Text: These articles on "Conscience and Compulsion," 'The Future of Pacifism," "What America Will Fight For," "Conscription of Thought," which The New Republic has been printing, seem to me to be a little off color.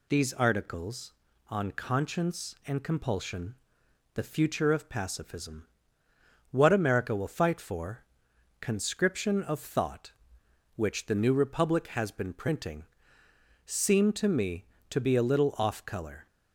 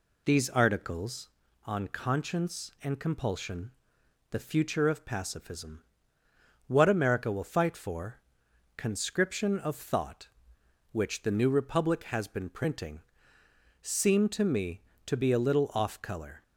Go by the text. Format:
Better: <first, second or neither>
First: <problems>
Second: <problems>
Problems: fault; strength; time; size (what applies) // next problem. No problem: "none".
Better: first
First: none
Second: starts louder than the rest; slight; until 1.4 s; 2 dB